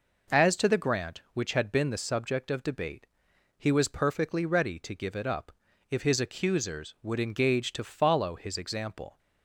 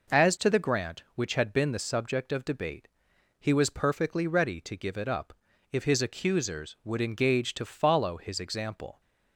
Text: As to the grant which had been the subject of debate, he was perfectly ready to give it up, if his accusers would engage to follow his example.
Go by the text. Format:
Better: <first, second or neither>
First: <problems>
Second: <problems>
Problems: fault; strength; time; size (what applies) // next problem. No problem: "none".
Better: neither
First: none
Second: none